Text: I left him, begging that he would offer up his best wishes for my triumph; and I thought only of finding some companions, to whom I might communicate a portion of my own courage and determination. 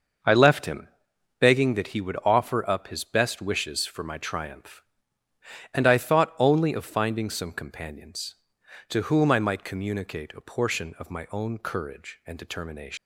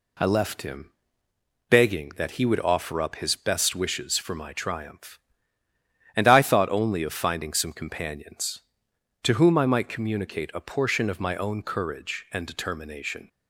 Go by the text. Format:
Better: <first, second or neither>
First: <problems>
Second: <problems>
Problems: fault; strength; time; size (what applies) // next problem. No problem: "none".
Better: second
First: starts louder than the rest; until 1.7 s; 6.5 dB // leaves "determination" unfinished; at 12.9 s; 120 ms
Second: none